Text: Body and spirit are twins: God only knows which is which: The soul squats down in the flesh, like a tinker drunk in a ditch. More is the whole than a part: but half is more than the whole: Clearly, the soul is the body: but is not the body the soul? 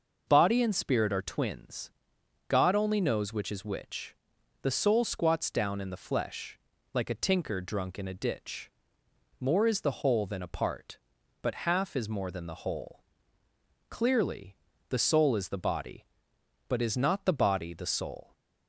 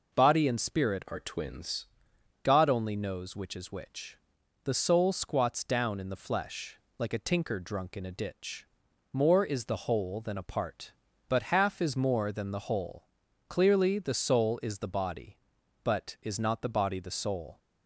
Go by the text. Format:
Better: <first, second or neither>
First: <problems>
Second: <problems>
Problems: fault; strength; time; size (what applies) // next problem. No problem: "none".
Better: first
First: none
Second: changes voice from "are" to "twins"; from 1.0 to 1.8 s; 0.8 s long